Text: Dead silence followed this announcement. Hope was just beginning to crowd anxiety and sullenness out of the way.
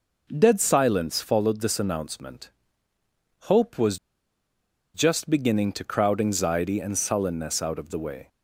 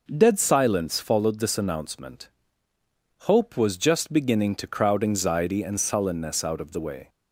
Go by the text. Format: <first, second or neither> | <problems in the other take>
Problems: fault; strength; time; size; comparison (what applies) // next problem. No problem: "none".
second | pauses between "was" and "just"; noticeable; at 3.9 s; 0.97 s long